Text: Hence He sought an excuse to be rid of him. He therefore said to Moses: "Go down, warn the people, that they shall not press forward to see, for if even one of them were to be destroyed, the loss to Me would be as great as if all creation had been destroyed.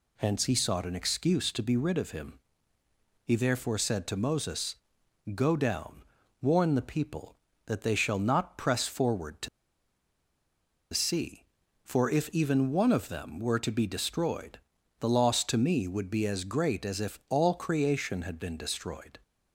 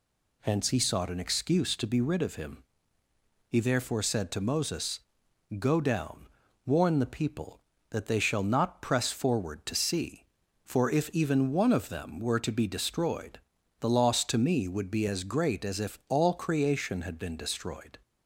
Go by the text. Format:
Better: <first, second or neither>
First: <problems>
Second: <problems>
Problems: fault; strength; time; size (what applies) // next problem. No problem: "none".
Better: second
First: pauses between "to" and "see"; strong; at 9.4 s; 1.4 s long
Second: none